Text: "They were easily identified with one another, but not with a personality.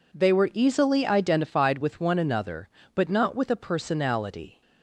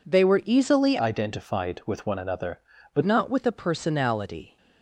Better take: first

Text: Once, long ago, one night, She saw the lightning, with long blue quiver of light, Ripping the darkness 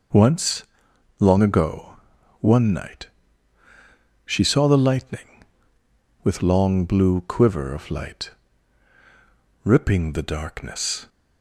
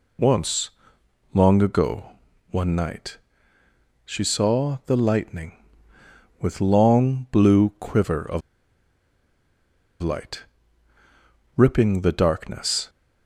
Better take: first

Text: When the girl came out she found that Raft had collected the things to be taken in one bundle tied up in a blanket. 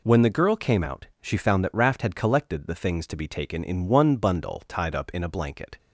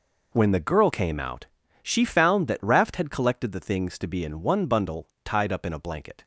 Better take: first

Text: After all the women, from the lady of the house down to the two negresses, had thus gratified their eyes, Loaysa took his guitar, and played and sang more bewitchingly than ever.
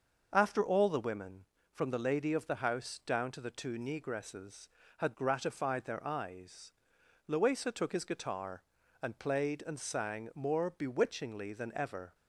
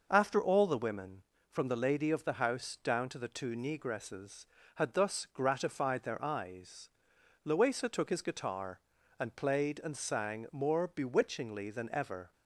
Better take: second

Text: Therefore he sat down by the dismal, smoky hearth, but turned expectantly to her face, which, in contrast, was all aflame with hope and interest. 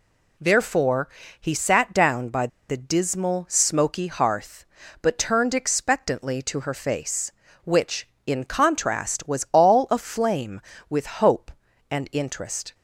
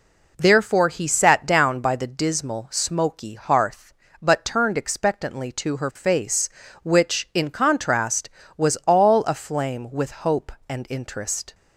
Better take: second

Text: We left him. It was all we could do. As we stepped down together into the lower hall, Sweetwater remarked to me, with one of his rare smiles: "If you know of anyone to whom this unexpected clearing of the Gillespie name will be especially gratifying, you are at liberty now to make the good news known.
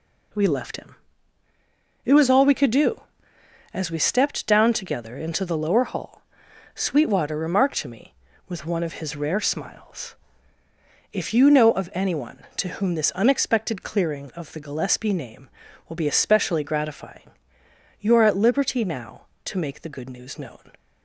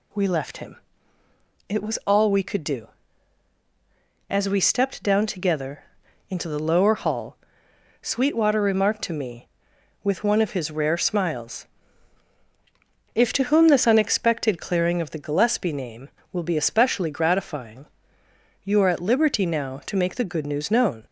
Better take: first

